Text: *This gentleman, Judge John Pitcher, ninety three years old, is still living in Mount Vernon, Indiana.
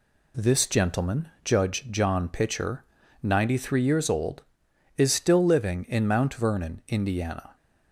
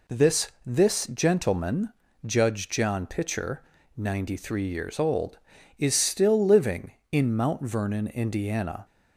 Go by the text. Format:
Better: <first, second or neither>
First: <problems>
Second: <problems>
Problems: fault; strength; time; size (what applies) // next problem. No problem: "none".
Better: first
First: none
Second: says "This" twice; at 0.6 s